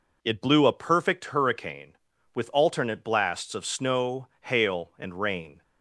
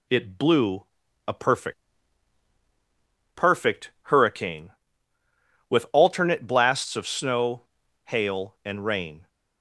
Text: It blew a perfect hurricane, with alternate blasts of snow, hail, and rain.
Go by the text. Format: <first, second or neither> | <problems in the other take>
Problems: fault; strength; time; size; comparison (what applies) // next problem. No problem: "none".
first | pauses between "blew" and "a"; at 0.8 s; 0.42 s long // says "perfect" twice; at 3.3 s